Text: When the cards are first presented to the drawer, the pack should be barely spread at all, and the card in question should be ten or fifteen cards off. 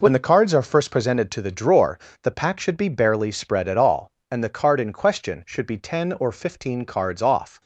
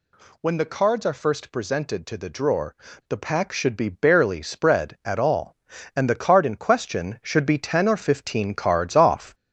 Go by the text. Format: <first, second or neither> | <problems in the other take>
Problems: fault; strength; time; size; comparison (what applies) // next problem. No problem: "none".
first | gets louder; throughout; 4 dB